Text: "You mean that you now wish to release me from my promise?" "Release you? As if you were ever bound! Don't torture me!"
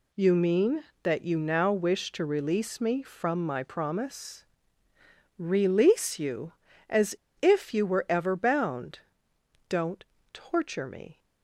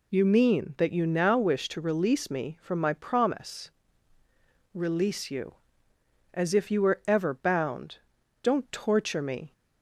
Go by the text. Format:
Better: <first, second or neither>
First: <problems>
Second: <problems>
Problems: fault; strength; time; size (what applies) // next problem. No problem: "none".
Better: second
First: pauses between "As" and "if"; slight; at 7.1 s; 0.24 s long // pauses between "Don't" and "torture"; slight; at 10.0 s; 0.28 s long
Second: none